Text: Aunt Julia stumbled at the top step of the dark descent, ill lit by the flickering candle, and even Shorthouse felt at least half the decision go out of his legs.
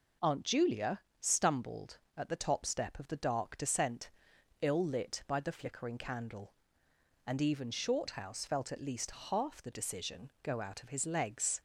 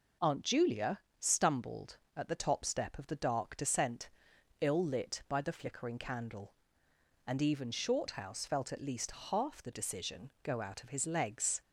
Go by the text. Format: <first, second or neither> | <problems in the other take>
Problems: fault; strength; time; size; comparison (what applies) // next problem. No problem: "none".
neither | pauses between "Julia" and "stumbled"; slight; the same in both // pauses between "least" and "half"; slight; the same in both